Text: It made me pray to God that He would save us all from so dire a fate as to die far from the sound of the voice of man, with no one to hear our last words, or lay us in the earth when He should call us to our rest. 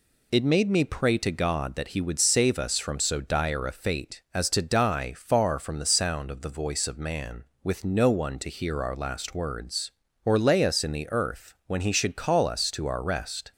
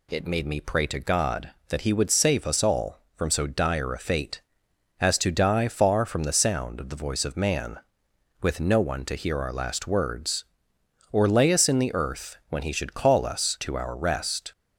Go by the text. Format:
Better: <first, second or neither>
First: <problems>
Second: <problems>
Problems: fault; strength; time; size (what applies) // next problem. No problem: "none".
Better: second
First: skips "all"; at 2.7 s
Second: none